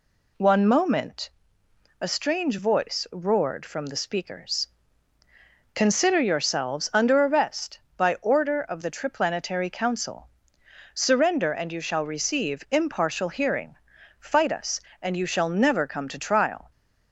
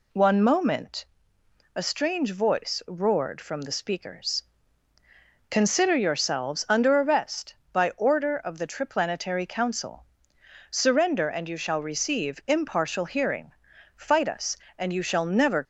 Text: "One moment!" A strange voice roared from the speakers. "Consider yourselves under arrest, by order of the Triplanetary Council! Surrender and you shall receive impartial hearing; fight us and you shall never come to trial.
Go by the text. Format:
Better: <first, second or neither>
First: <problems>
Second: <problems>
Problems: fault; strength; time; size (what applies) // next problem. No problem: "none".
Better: first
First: none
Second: stops before "come to trial"; at 15.6 s